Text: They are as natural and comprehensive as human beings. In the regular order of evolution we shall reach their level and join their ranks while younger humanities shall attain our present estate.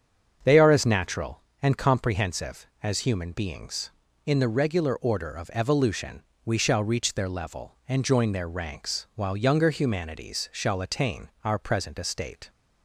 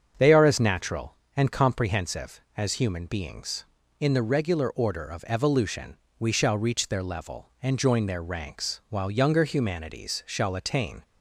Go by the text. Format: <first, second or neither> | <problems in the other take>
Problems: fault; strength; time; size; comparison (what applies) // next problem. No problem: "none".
first | starts louder than the rest; strong; until 1.3 s; 7 dB; strong in the first // pauses between "evolution" and "we"; slight; at 5.9 s; 0.22 s long; slight in the first // stops before "our present estate"; at 11.0 s